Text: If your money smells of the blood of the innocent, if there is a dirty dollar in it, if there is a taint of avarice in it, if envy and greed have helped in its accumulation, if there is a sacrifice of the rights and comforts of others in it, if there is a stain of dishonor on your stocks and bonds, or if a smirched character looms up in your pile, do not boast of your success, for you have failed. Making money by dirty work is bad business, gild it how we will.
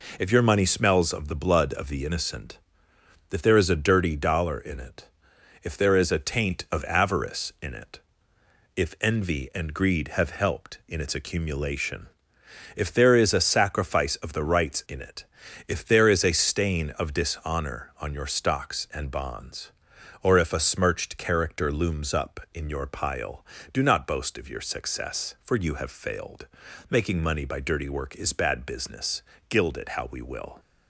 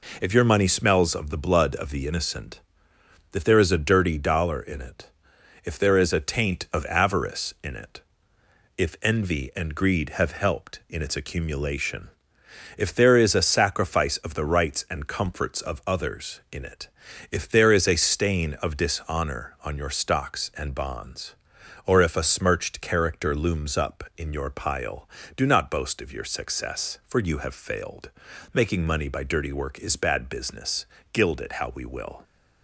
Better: second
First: skips "and comforts of others"; at 14.8 s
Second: none

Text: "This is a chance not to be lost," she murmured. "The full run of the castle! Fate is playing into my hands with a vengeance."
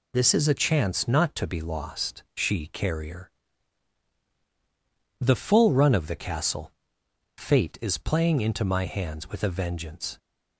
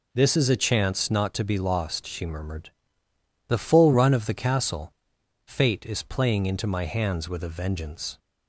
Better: second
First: says "carrier" for "murmured"; at 2.6 s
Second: none

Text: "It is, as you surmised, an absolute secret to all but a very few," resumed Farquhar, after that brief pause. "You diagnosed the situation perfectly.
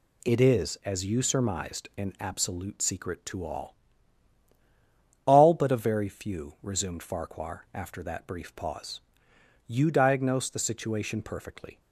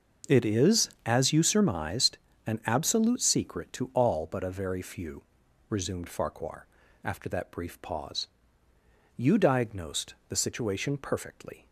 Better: second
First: says "all" twice; at 5.2 s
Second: none

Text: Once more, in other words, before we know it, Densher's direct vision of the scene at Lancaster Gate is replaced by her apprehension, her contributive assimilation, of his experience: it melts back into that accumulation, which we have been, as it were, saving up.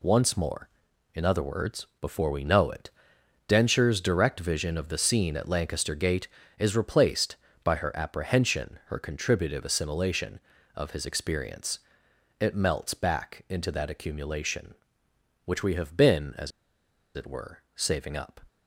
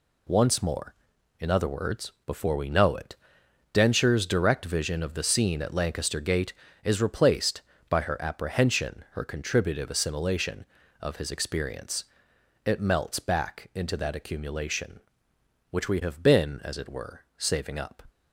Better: second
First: pauses between "as" and "it"; noticeable; at 16.5 s; 0.64 s long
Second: none

